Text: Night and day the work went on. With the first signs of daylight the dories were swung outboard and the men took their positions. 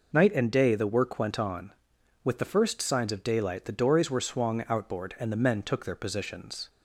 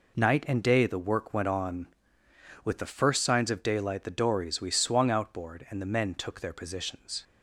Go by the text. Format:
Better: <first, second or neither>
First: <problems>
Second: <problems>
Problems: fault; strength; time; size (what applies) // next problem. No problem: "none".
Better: first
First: none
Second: says "we" for "were"; at 4.5 s